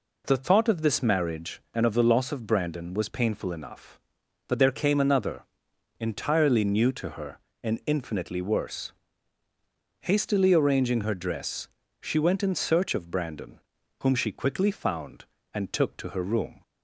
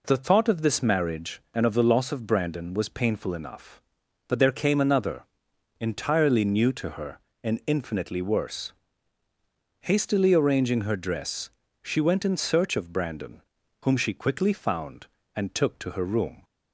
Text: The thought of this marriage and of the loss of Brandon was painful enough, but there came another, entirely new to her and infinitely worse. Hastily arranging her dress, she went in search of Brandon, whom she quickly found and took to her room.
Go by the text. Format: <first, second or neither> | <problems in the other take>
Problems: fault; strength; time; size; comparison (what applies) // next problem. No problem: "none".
neither | none